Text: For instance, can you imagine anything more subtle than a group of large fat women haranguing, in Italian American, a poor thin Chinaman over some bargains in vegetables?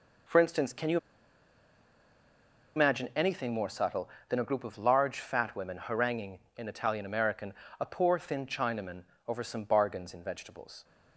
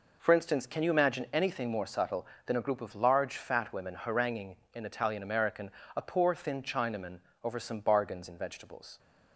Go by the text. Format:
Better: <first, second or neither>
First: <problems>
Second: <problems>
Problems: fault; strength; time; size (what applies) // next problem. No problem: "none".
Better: second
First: pauses between "you" and "imagine"; strong; at 0.9 s; 1.7 s long // pauses between "Chinaman" and "over"; slight; at 9.0 s; 0.22 s long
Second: pauses between "Chinaman" and "over"; slight; at 7.1 s; 0.22 s long